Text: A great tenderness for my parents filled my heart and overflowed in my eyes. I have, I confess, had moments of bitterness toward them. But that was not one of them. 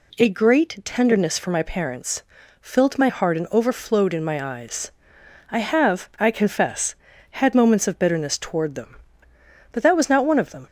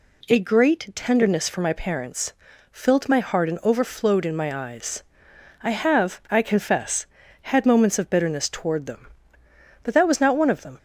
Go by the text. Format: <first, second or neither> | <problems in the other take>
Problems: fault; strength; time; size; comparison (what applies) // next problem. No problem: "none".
neither | pauses between "parents" and "filled"; the same in both